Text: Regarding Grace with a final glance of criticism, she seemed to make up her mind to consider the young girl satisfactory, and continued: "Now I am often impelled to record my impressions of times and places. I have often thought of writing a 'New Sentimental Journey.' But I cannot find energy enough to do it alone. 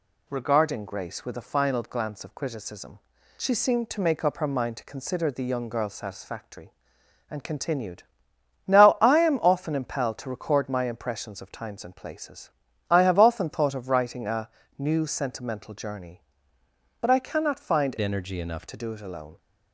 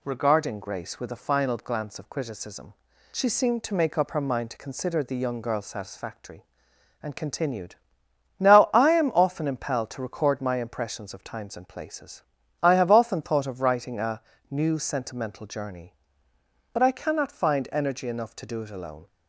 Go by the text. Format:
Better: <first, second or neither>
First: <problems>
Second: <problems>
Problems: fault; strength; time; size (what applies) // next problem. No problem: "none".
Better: second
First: pauses between "a" and "New"; slight; at 14.4 s; 0.28 s long // changes voice from "energy" to "enough"; from 17.9 to 18.6 s; 0.7 s long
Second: pauses between "a" and "New"; slight; at 14.2 s; 0.28 s long